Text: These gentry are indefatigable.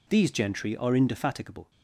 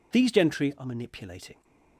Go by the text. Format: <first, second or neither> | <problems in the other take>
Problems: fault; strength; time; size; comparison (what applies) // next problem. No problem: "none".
first | says "manipulating" for "indefatigable"; at 0.8 s